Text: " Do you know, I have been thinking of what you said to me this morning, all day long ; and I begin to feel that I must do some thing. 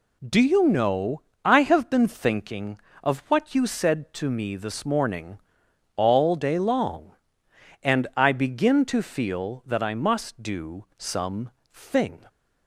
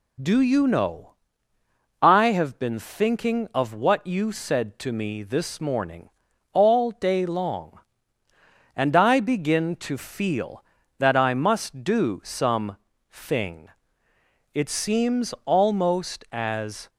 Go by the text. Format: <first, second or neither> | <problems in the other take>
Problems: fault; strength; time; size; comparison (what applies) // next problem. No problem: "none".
first | pauses between "some" and "thing"; slight; at 12.7 s; 0.34 s long; slight in the first // goes on to say "It seems almost as"; strong; from 14.5 s on; 2.3 s long